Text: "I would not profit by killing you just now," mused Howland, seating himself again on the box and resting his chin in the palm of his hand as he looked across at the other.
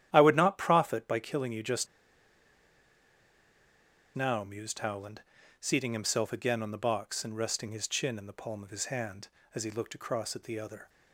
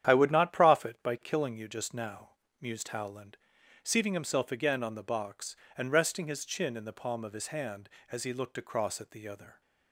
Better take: second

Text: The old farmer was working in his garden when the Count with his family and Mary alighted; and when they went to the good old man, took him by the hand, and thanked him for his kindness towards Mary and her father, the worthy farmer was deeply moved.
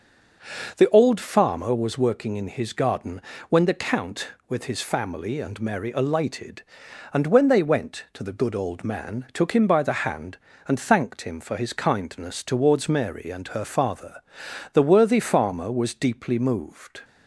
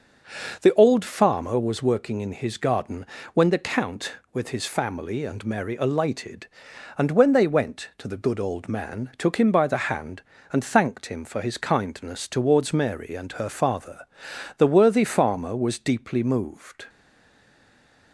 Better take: first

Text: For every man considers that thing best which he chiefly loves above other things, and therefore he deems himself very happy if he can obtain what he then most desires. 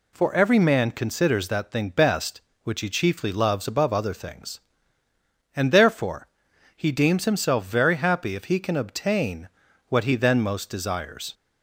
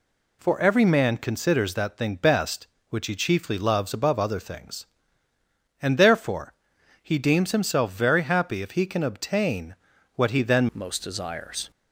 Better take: first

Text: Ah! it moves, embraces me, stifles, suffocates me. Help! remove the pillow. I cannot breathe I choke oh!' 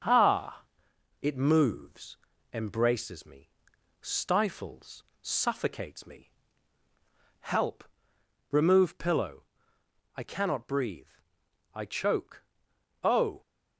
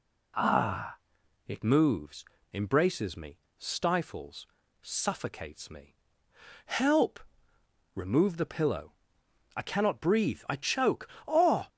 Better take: second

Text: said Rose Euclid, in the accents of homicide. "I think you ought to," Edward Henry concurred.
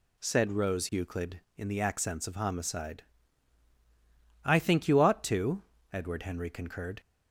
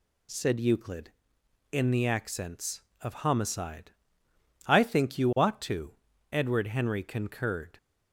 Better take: first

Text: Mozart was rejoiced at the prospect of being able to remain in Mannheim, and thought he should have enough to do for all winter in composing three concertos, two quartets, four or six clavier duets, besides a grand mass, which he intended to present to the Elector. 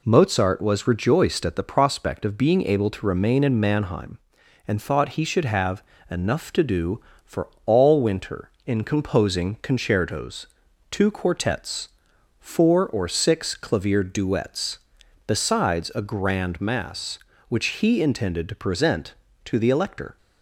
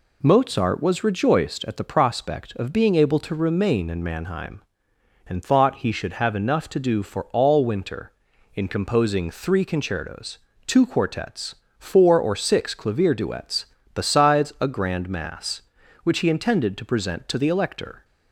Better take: second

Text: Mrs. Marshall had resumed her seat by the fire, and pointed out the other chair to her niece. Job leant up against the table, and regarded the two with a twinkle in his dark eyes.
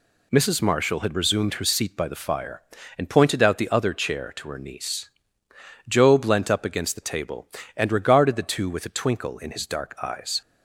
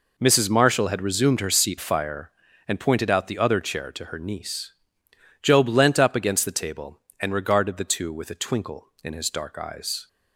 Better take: first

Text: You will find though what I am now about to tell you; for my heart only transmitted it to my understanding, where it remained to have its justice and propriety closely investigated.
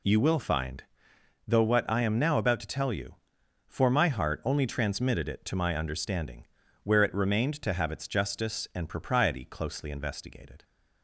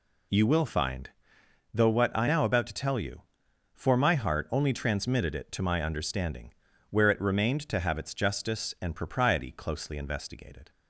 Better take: first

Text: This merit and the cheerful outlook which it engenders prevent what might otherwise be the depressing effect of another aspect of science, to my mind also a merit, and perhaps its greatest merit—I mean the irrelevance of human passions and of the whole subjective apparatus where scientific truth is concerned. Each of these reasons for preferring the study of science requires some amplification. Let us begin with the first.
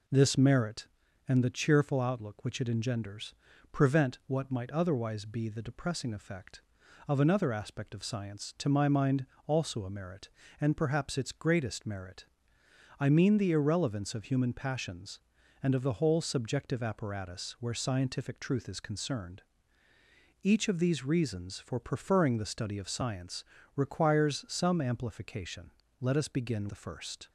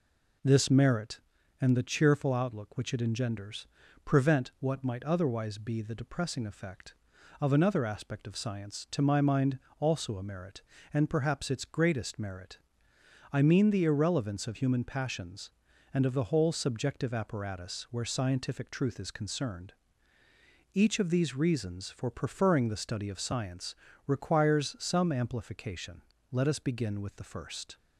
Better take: second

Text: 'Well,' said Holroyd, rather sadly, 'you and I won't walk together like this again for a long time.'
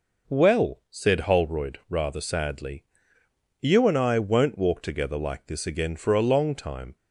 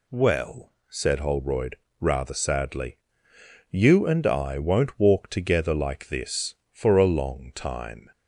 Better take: first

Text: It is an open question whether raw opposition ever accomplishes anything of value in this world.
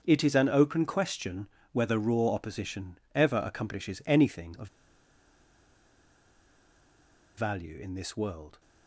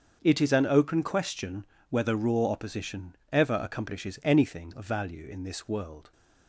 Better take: second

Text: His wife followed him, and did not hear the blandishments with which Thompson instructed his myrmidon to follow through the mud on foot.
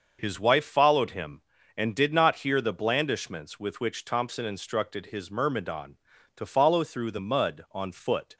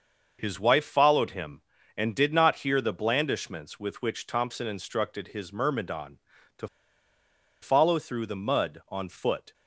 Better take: first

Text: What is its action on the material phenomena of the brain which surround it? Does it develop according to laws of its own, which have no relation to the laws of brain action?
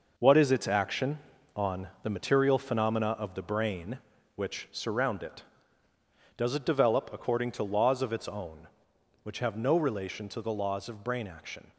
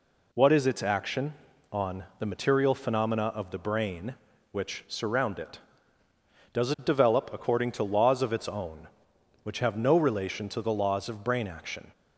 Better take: second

